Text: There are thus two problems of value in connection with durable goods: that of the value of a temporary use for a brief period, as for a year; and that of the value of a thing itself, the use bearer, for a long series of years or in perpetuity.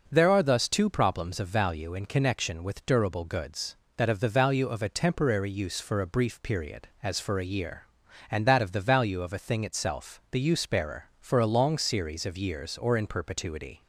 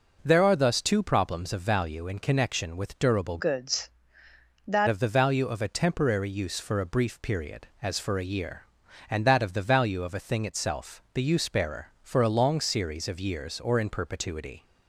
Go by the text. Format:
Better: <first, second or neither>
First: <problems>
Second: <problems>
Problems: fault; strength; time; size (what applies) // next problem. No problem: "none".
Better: first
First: none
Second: changes voice from "goods" to "that"; from 3.3 to 4.8 s; 1.5 s long